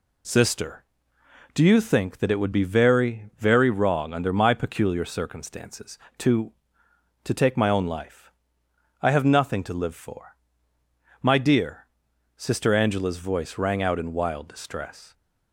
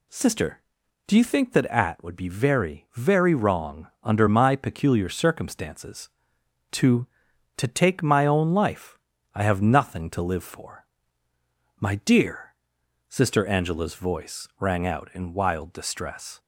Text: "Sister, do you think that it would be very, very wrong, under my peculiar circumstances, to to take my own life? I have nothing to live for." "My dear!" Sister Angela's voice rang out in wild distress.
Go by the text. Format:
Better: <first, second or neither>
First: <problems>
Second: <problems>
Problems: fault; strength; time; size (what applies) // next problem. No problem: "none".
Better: first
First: none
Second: says "at" for "it"; at 1.6 s